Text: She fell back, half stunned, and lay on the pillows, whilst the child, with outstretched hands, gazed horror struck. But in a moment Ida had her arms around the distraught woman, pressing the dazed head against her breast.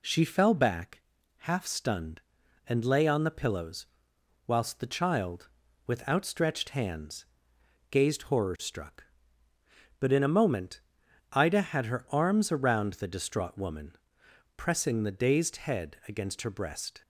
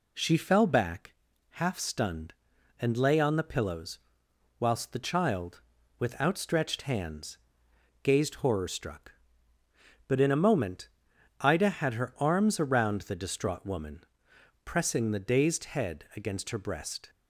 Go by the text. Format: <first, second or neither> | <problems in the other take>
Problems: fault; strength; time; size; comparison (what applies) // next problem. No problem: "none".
neither | pauses between "moment" and "Ida"; noticeable; the same in both